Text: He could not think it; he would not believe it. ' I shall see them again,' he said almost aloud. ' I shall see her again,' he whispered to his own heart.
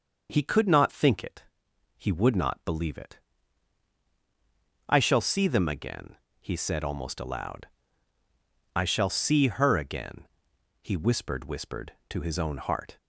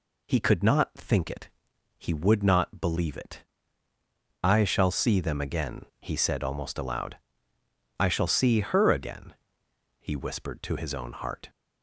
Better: second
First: says "whispered" twice; at 11.4 s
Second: none

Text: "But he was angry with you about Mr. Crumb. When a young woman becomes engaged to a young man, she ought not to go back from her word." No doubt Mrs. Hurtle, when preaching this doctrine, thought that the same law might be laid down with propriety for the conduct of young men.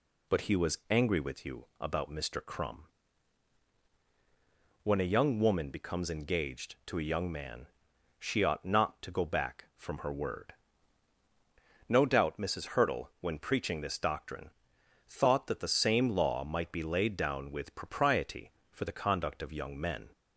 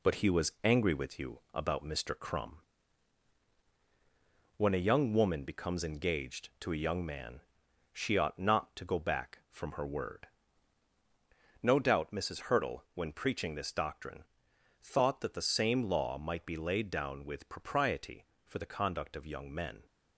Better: first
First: none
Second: gets quieter; noticeable; throughout; 5 dB

